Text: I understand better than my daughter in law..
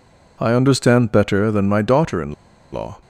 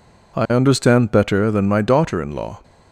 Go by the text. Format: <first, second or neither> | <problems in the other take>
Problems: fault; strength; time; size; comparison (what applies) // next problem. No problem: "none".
second | pauses between "in" and "law"; at 2.3 s; 0.39 s long